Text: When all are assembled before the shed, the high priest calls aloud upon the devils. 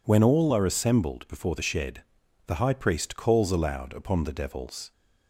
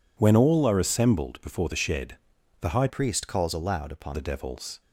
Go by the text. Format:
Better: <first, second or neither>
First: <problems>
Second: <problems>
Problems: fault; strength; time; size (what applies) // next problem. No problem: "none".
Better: first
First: none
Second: changes voice from "priest" to "upon"; from 2.8 to 4.1 s; 1.3 s long